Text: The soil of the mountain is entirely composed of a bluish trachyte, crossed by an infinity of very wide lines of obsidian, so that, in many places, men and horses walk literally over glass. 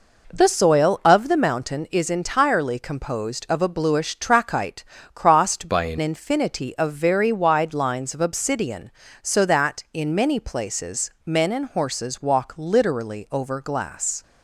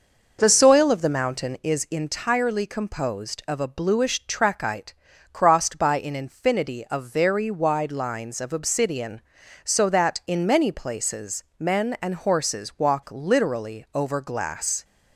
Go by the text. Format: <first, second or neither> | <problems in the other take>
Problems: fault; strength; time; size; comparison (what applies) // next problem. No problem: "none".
second | changes voice from "by" to "an"; from 5.6 to 5.9 s; 0.3 s long